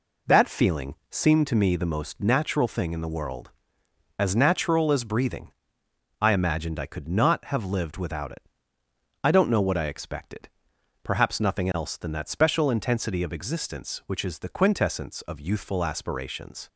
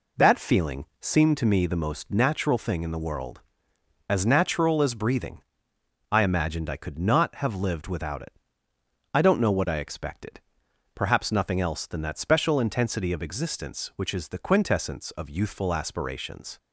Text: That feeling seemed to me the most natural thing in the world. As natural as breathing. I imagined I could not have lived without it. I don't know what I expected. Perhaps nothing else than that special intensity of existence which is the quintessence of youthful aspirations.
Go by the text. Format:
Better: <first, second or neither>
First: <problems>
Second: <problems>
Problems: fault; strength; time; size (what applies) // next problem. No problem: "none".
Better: neither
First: pauses between "feeling" and "seemed"; slight; at 0.9 s; 0.16 s long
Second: pauses between "feeling" and "seemed"; slight; at 0.8 s; 0.16 s long